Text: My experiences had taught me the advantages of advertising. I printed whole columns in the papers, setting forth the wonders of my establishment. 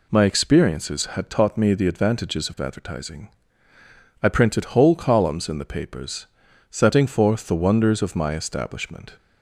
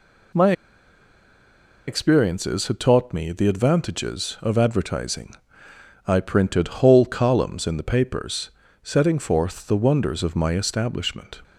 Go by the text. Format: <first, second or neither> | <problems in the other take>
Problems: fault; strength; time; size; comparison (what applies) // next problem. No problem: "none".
first | pauses between "My" and "experiences"; strong; at 0.5 s; 1.3 s long